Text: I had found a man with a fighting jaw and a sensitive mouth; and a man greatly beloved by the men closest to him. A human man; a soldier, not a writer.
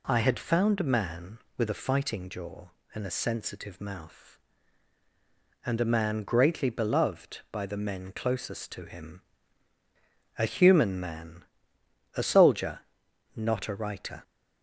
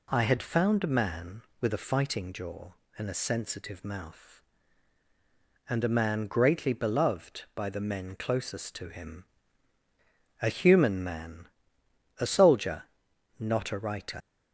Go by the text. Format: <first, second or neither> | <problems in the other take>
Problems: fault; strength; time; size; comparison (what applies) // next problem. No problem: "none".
first | leaves "writer" unfinished; at 14.2 s; 55 ms